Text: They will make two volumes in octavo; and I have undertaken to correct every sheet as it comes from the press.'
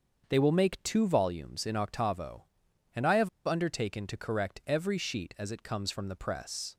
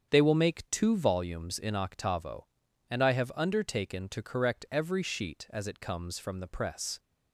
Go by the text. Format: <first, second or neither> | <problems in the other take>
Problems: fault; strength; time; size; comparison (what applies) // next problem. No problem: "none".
second | starts louder than the rest; until 1.2 s; 6.5 dB; strong in the second // pauses between "have" and "undertaken"; slight; at 3.2 s; 0.16 s long